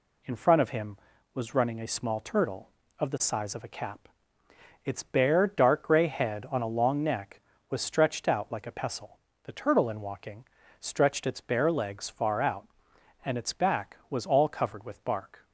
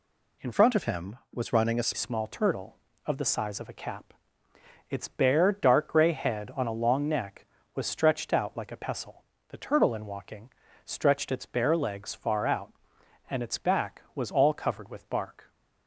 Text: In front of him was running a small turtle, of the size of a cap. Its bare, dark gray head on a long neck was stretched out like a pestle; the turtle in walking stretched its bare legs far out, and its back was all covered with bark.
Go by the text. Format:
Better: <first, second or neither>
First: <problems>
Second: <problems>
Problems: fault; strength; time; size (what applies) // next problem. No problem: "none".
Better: first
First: pauses between "walking" and "stretched"; slight; at 10.4 s; 0.36 s long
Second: changes voice from "front" to "a"; from 0.5 to 1.9 s; 1.4 s long // pauses between "walking" and "stretched"; slight; at 10.4 s; 0.36 s long